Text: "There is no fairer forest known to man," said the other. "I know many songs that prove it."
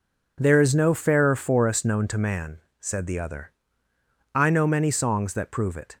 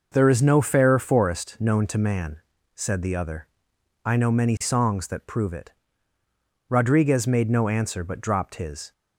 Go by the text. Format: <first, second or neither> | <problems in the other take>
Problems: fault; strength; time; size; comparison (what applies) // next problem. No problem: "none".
first | goes on to say "Rodriguez made no answer but dropped his"; strong; from 6.6 s on; 2.2 s long